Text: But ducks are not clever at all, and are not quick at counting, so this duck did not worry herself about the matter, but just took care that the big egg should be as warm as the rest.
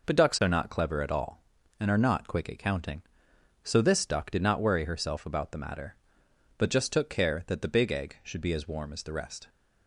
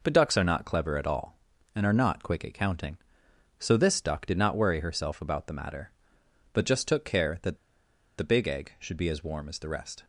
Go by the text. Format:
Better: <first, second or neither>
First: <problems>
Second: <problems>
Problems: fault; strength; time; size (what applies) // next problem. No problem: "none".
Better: first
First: none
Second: pauses between "that" and "the"; noticeable; at 7.5 s; 0.62 s long